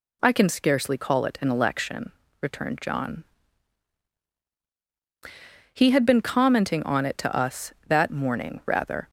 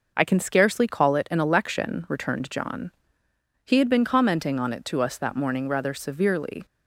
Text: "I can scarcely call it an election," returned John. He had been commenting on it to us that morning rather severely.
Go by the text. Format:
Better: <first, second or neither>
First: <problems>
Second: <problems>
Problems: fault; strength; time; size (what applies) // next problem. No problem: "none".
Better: second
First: stops before "severely"; at 9.0 s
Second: none